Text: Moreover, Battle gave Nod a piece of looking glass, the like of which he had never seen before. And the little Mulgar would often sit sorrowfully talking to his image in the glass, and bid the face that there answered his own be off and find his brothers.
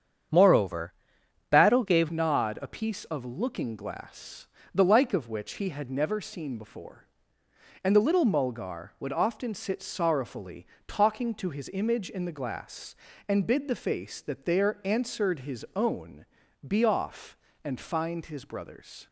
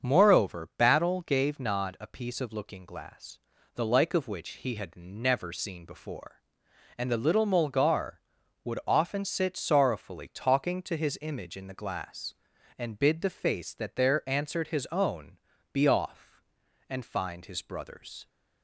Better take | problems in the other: second | starts louder than the rest; strong; until 1.8 s; 8 dB; also in the second // changes voice at "Nod"; from 2.1 s on; 16.9 s long // pauses between "sorrowfully" and "talking"; slight; at 10.6 s; 0.22 s long // pauses between "own" and "be"; at 16.2 s; 0.40 s long; slight in the second

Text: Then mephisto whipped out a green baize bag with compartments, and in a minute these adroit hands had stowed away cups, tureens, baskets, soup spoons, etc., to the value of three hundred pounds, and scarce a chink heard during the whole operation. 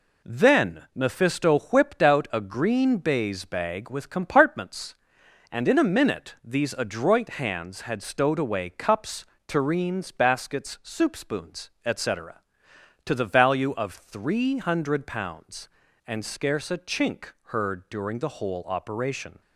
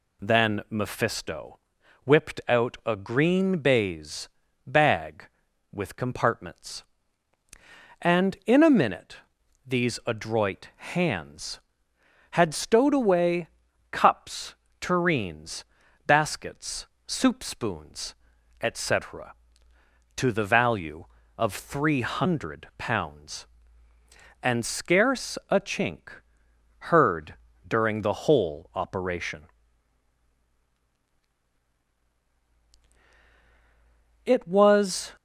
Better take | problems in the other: first | pauses between "mephisto" and "whipped"; at 1.5 s; 0.44 s long // pauses between "baize" and "bag"; at 4.2 s; 0.38 s long // pauses between "minute" and "these"; noticeable; at 9.1 s; 0.50 s long // pauses between "away" and "cups"; at 13.4 s; 0.44 s long // pauses between "chink" and "heard"; noticeable; at 26.0 s; 0.68 s long // pauses between "heard" and "during"; slight; at 27.3 s; 0.34 s long // goes on to say "It was"; noticeable; from 34.2 s on; 0.90 s long

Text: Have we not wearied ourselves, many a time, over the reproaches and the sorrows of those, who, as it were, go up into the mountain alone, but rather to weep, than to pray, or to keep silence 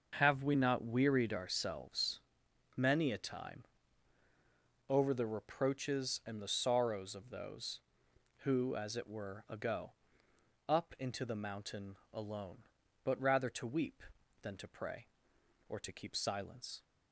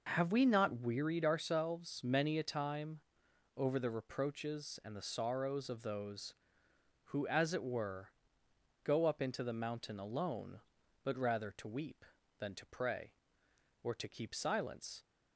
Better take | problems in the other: second | starts louder than the rest; until 1.1 s; 6.5 dB // says "ago" for "go"; at 9.4 s // pauses between "mountain" and "alone"; slight; at 11.9 s; 0.18 s long

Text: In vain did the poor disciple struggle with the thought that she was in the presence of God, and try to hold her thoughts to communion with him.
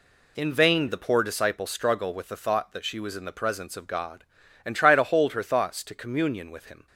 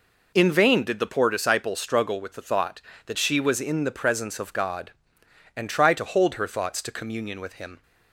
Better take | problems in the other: second | skips "did"; at 0.8 s

